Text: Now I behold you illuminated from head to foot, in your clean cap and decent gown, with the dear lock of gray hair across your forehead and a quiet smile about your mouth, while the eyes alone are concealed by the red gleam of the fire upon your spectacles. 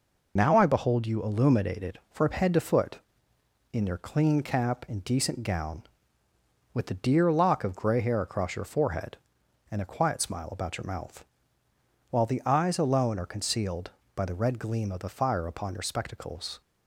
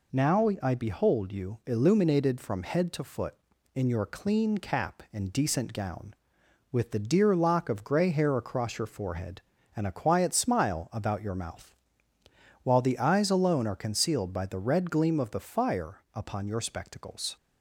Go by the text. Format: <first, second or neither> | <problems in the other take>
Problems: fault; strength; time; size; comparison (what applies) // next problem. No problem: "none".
second | loses the start of "Now"; at 0.3 s; 70 ms